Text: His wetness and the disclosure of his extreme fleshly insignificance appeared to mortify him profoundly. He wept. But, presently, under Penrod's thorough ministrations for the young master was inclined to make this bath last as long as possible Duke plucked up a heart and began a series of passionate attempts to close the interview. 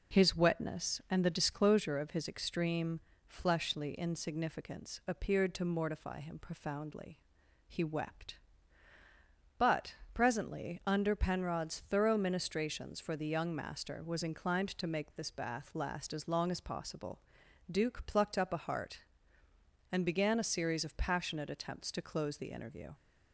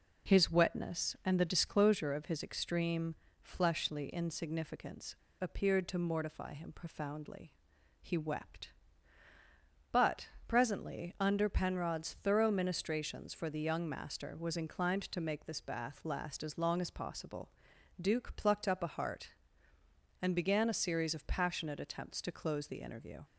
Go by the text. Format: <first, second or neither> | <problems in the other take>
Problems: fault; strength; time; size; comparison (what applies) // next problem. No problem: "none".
first | pauses between "extreme" and "fleshly"; slight; at 3.1 s; 0.26 s long; slight in the first // pauses between "insignificance" and "appeared"; slight; at 5.1 s; 0.26 s long // pauses between "possible" and "Duke"; noticeable; at 17.4 s; 0.50 s long; noticeable in the first